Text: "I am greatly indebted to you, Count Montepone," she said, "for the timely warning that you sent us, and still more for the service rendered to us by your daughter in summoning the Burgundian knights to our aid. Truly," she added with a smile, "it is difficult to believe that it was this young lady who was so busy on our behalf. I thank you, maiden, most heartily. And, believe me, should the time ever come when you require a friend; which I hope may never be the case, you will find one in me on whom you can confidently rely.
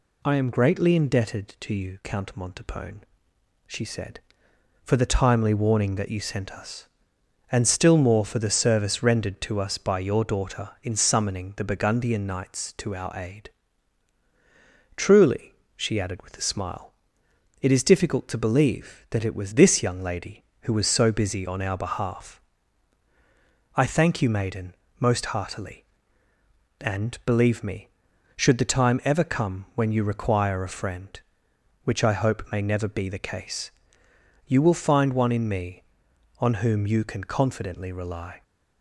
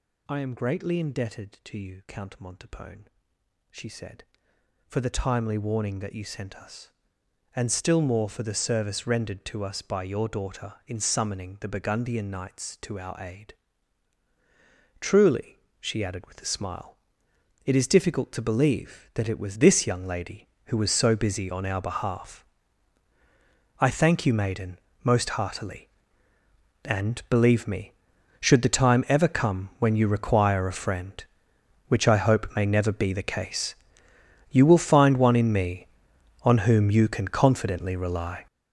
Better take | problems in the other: first | gets louder; strong; throughout; 11.5 dB

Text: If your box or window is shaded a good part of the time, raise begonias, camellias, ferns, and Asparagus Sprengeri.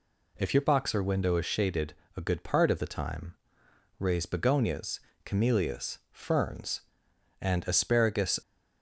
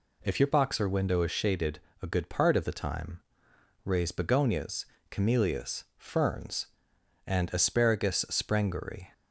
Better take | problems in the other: second | pauses between "shaded" and "a"; slight; at 1.9 s; 0.24 s long; slight in the second // stops before "Sprengeri"; at 8.4 s

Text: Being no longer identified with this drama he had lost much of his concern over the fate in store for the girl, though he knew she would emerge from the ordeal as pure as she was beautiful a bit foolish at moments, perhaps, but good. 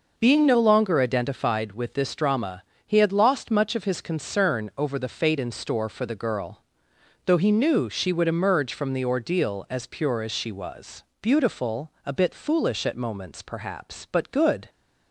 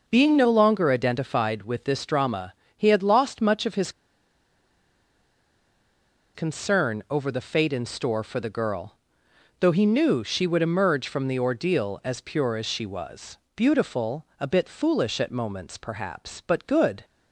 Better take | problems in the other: first | pauses between "drama" and "he"; slight; at 2.5 s; 0.24 s long; slight in the first // pauses between "his" and "concern"; strong; at 3.9 s; 2.4 s long // pauses between "was" and "beautiful"; slight; at 13.3 s; 0.18 s long; slight in the first // pauses between "beautiful" and "a"; slight; at 14.2 s; 0.16 s long; slight in the first

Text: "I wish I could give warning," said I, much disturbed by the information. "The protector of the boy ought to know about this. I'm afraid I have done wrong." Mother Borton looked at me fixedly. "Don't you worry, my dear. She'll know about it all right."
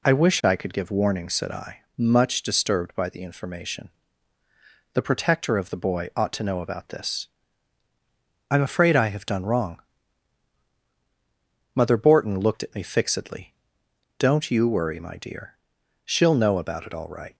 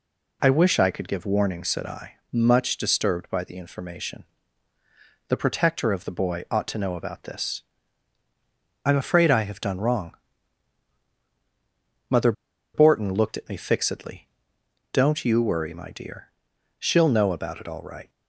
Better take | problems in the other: first | pauses between "Mother" and "Borton"; at 12.3 s; 0.42 s long

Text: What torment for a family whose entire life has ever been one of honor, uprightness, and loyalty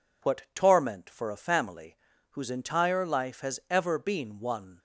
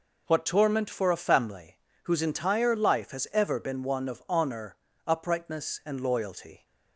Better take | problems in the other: second | pauses between "family" and "whose"; slight; at 1.9 s; 0.34 s long; slight in the second // stops before "of honor uprightness and loyalty"; at 4.7 s

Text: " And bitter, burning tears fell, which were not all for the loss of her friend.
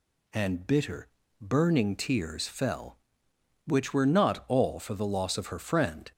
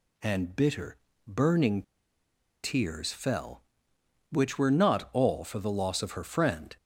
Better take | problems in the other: first | pauses between "burning" and "tears"; noticeable; at 1.8 s; 0.81 s long

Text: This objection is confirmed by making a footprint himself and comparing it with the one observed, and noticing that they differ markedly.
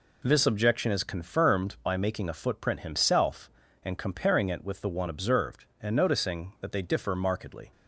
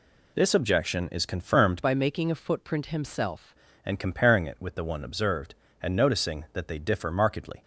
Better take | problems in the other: first | changes voice from "by" to "himself"; from 1.8 to 3.5 s; 1.7 s long

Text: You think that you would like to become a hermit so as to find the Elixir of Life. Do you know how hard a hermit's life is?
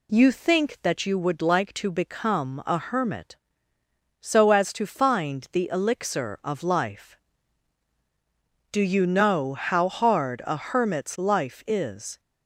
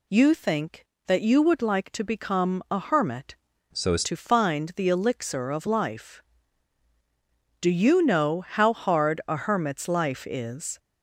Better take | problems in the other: first | changes voice from "so" to "as"; from 3.7 to 4.0 s; 0.3 s long

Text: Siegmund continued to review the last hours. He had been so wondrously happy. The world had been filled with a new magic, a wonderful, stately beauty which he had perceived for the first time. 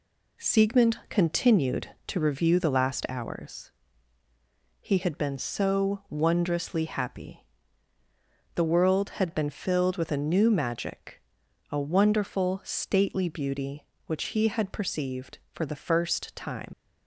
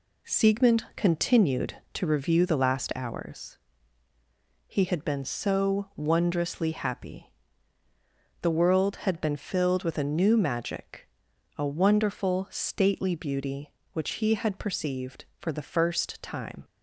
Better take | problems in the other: second | leaves "time" unfinished; at 16.7 s; 45 ms

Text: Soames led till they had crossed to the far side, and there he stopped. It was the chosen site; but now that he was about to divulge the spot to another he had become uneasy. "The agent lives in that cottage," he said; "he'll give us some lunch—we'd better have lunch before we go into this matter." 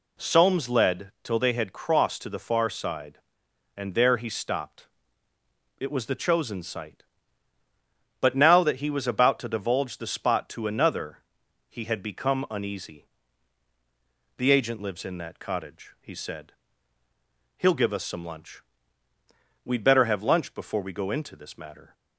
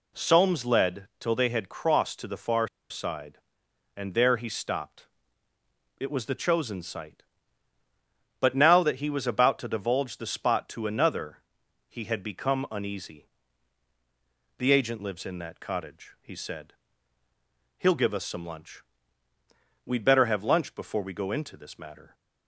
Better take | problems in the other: first | pauses between "far" and "side"; slight; at 2.6 s; 0.21 s long // pauses between "another" and "he"; noticeable; at 11.3 s; 0.50 s long; noticeable in the first

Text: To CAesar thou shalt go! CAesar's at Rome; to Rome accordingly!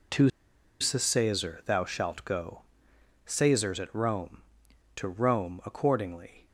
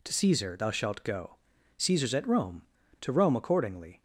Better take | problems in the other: second | pauses between "To" and "CAesar"; noticeable; at 0.2 s; 0.51 s long

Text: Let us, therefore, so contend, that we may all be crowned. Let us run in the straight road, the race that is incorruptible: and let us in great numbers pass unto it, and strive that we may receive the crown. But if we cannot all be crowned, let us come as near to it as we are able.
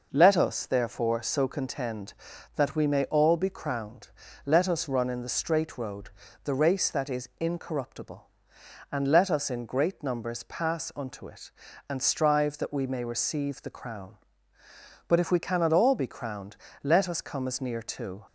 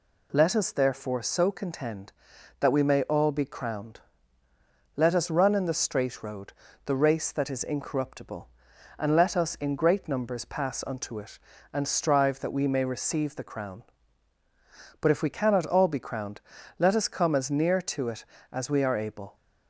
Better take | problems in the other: second | stops before "it as we are able"; at 18.2 s

